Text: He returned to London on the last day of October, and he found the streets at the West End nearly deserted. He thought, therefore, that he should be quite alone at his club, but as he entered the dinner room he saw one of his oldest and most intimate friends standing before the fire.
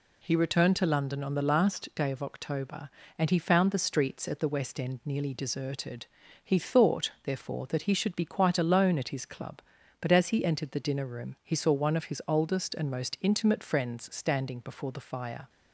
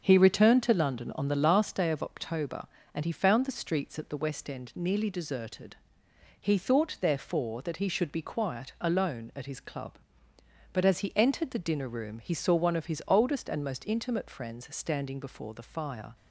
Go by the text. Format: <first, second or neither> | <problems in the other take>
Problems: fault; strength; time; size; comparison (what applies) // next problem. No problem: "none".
first | starts louder than the rest; until 1.0 s; 6.5 dB // says "quiet" for "quite"; at 8.2 s